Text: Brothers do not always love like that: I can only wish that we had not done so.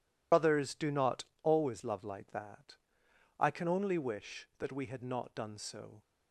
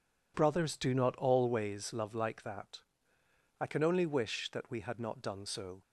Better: second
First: loses the start of "Brothers"; at 0.3 s; 75 ms // pauses between "not" and "always"; slight; at 1.2 s; 0.18 s long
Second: none

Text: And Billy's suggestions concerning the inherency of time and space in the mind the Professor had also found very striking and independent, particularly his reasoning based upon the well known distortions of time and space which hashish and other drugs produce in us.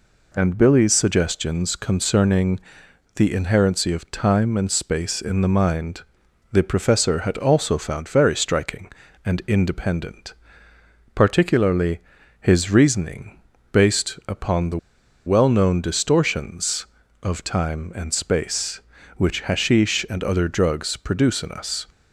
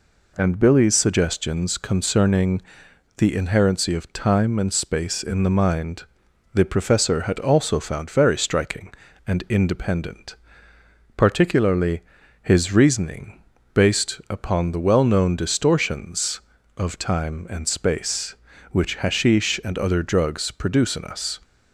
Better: second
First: pauses between "concerning" and "the"; noticeable; at 2.5 s; 0.58 s long // pauses between "mind" and "the"; noticeable; at 6.0 s; 0.48 s long // pauses between "particularly" and "his"; at 11.9 s; 0.42 s long // pauses between "reasoning" and "based"; slight; at 13.3 s; 0.34 s long // pauses between "the" and "well"; noticeable; at 14.7 s; 0.49 s long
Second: pauses between "concerning" and "the"; noticeable; at 2.6 s; 0.58 s long // pauses between "mind" and "the"; noticeable; at 6.0 s; 0.48 s long // pauses between "particularly" and "his"; at 12.0 s; 0.42 s long // pauses between "reasoning" and "based"; slight; at 13.4 s; 0.34 s long

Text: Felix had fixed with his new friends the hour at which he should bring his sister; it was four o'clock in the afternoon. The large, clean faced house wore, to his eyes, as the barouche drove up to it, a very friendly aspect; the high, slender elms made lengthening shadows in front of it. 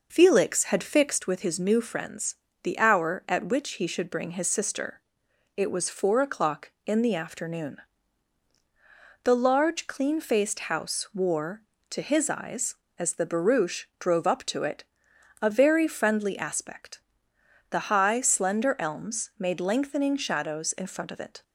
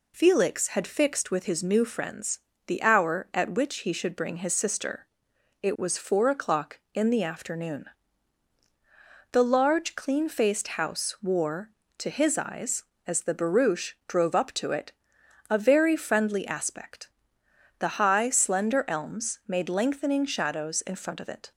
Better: second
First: starts louder than the rest; noticeable; until 1.2 s; 5 dB // pauses between "friends" and "the"; slight; at 2.3 s; 0.28 s long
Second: pauses between "friends" and "the"; slight; at 2.3 s; 0.28 s long

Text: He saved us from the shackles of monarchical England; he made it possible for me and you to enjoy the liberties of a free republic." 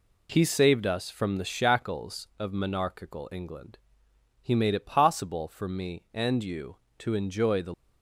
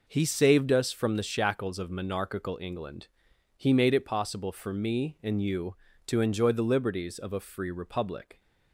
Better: second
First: stops before "liberties of a free republic"; at 7.7 s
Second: none

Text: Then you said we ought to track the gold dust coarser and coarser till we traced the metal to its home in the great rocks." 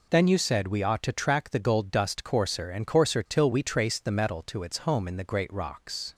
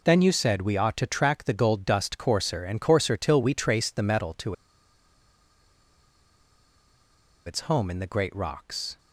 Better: first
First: none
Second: pauses between "to" and "its"; strong; at 4.5 s; 2.9 s long

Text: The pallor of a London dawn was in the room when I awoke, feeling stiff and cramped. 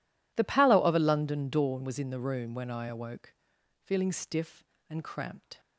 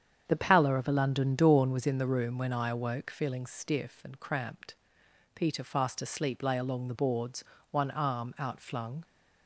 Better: first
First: none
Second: starts louder than the rest; strong; until 1.3 s; 8 dB // goes on to say "Peter fast asleep lay along the boards one arm outflung"; strong; from 5.3 s on; 3.6 s long

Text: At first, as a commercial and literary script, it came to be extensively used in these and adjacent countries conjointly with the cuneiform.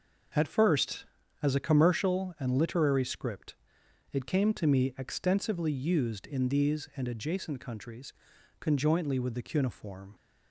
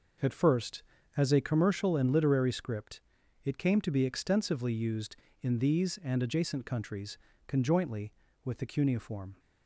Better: second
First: says "me" for "be"; at 4.6 s // pauses between "countries" and "conjointly"; noticeable; at 8.1 s; 0.46 s long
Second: pauses between "countries" and "conjointly"; slight; at 7.1 s; 0.30 s long

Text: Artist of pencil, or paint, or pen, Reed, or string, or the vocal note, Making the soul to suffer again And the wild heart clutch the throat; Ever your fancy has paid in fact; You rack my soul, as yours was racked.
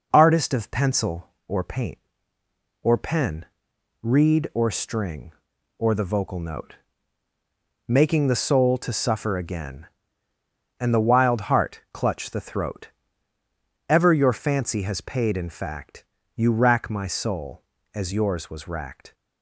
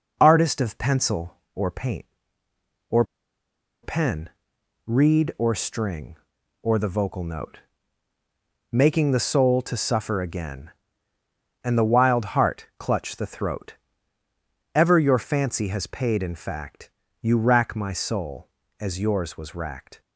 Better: first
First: none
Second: pauses between "or" and "pen"; noticeable; at 3.0 s; 0.79 s long

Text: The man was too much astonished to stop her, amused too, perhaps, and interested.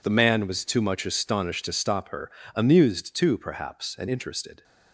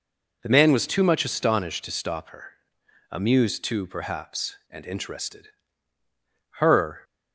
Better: first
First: none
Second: goes on to say "Her"; slight; from 6.5 s on; 0.44 s long

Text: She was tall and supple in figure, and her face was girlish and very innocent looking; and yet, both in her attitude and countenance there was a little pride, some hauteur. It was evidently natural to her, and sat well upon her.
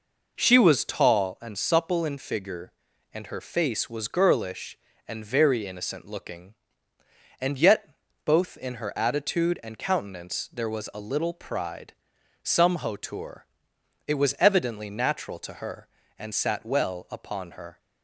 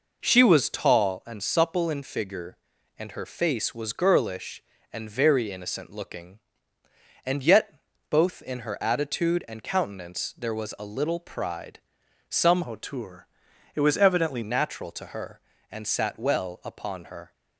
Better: first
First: none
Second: changes voice from "hauteur" to "evidently"; from 12.6 to 14.4 s; 1.8 s long

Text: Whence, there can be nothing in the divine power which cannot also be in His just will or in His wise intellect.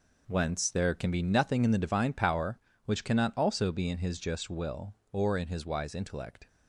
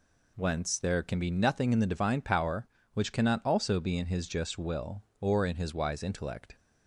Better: second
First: gets quieter; strong; throughout; 9.5 dB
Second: none

